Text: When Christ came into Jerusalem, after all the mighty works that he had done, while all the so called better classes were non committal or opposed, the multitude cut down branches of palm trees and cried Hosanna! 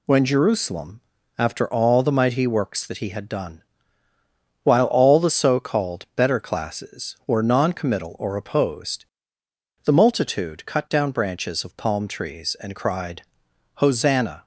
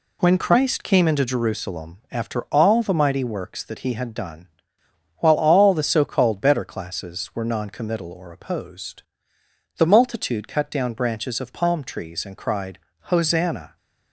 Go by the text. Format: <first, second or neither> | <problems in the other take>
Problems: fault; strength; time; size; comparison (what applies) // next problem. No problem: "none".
second | skips "Christ came into"; at 0.2 s // pauses between "cried" and "Hosanna"; noticeable; at 13.2 s; 0.52 s long; slight in the second